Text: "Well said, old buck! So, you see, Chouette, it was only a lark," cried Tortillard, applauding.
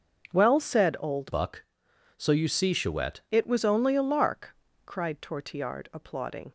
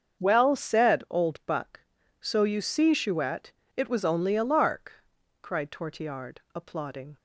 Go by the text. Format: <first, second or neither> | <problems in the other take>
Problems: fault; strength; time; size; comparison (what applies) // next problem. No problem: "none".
second | starts louder than the rest; until 1.3 s; 6.5 dB; also in the second // changes voice from "buck" to "Chouette"; from 1.3 to 3.2 s; 1.9 s long